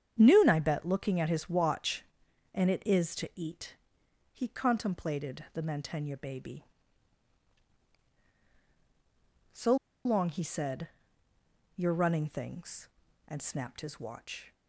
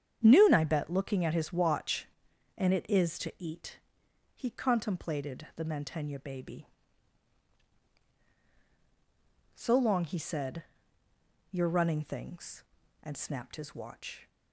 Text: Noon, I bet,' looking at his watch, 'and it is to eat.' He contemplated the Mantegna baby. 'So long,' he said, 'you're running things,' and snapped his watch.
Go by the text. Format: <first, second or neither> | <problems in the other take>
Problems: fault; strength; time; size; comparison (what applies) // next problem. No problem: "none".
second | starts louder than the rest; strong; until 1.2 s; 8.5 dB; strong in the second // pauses between "So" and "long"; slight; at 9.7 s; 0.29 s long